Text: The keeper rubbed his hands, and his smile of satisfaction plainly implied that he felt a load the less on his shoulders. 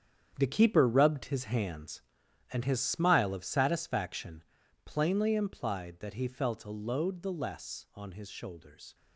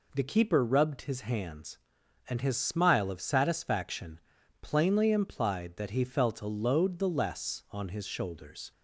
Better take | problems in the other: second | gets quieter; strong; throughout; 11 dB // pauses between "satisfaction" and "plainly"; at 4.4 s; 0.42 s long; also in the second

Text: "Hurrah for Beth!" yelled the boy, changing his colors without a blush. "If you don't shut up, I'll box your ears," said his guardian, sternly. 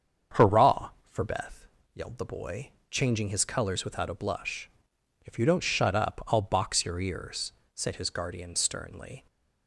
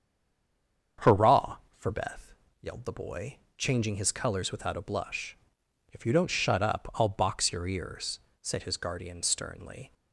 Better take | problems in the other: first | stays silent before the first word; slight; until 0.9 s; 0.9 s long // starts louder than the rest; strong; until 2.2 s; 7.5 dB; strong in the first

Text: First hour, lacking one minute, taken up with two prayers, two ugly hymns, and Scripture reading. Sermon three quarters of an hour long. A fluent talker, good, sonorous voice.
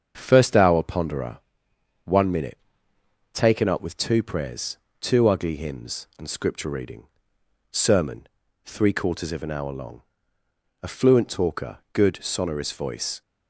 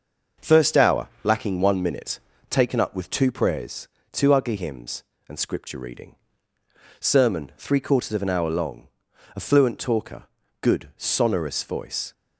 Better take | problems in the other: second | starts louder than the rest; strong; until 1.1 s; 7 dB; also in the second // says "ponderer" for "lacking"; at 0.8 s // pauses between "Sermon" and "three"; at 8.2 s; 0.40 s long

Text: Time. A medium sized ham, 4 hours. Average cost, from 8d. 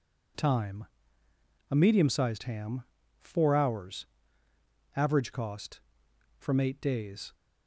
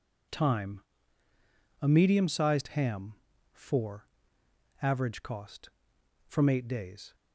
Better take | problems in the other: first | skips "hours"; at 4.4 s

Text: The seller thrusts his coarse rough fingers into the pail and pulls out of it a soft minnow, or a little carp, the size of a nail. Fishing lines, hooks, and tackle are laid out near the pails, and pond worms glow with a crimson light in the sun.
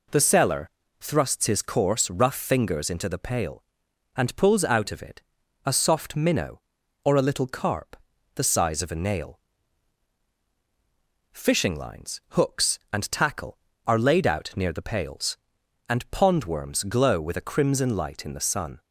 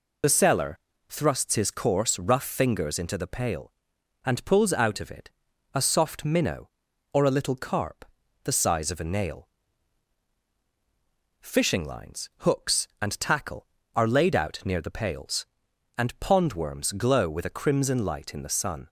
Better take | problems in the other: first | loses the start of "The"; at 0.2 s; 50 ms // pauses between "seller" and "thrusts"; slight; at 0.7 s; 0.32 s long; slight in the first // pauses between "it" and "a"; noticeable; at 5.2 s; 0.46 s long; noticeable in the first

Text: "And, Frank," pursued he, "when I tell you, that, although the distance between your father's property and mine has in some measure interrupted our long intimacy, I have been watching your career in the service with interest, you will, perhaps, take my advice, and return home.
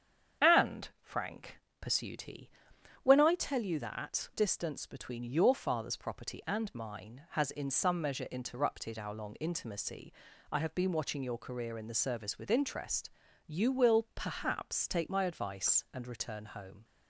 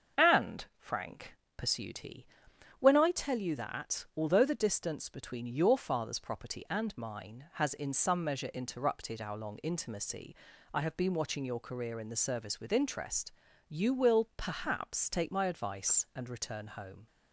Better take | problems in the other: second | starts louder than the rest; strong; until 1.5 s; 7.5 dB; also in the second // skips "although the"; at 4.3 s

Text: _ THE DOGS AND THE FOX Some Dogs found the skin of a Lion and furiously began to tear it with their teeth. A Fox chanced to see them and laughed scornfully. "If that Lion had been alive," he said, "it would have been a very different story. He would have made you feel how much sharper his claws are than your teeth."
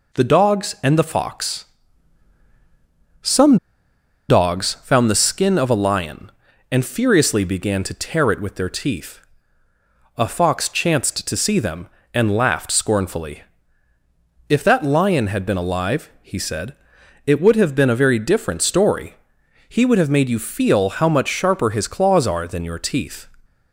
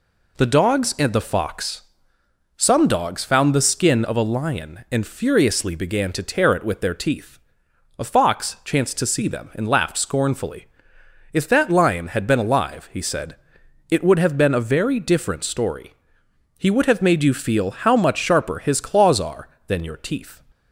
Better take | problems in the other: second | pauses between "FOX" and "Some"; strong; at 1.6 s; 1.5 s long; noticeable in the second // pauses between "Some" and "Dogs"; noticeable; at 3.5 s; 0.73 s long

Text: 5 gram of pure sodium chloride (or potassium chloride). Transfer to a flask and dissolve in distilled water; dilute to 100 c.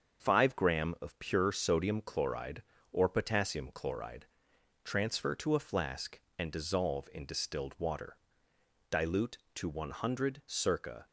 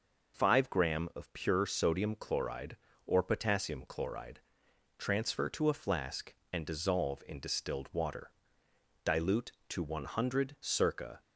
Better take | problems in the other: second | gets quieter; noticeable; throughout; 5.5 dB

